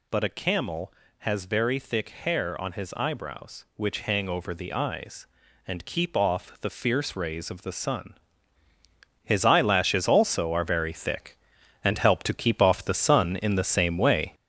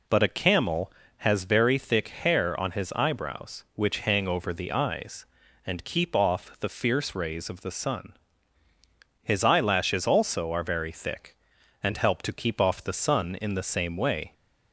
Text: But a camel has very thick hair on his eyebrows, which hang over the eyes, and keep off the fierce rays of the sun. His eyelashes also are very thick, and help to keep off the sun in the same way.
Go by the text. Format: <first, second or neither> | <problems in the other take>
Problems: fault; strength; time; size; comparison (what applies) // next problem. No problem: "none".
second | gets louder; throughout; 6 dB